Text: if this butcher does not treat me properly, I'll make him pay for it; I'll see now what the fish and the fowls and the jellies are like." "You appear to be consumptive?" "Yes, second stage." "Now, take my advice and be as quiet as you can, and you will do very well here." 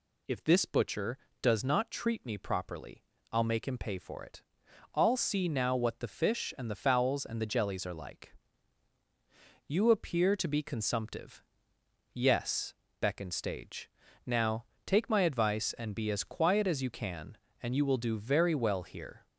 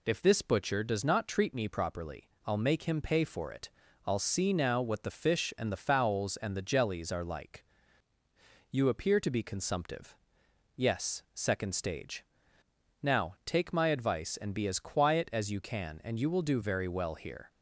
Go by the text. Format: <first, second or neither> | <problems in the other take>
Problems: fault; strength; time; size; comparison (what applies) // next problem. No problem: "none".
second | says "beckoned" for "second"; at 13.0 s